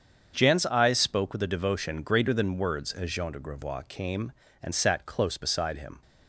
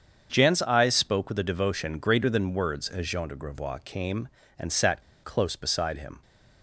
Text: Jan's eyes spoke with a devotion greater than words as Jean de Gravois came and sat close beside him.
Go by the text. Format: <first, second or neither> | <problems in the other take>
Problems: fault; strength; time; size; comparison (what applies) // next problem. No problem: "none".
first | starts louder than the rest; strong; until 1.3 s; 7.5 dB; strong in the first // pauses between "sat" and "close"; slight; at 5.0 s; 0.21 s long